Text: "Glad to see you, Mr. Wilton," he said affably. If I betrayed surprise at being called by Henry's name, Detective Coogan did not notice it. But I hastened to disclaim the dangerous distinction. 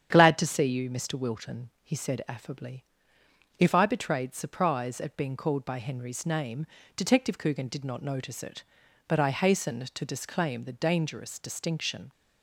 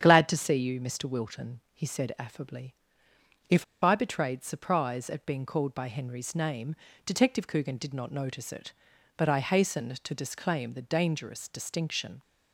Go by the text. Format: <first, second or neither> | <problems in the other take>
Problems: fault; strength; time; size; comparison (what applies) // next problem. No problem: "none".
first | starts louder than the rest; strong; until 1.0 s; 8.5 dB; strong in the first // pauses between "If" and "I"; slight; at 3.6 s; 0.20 s long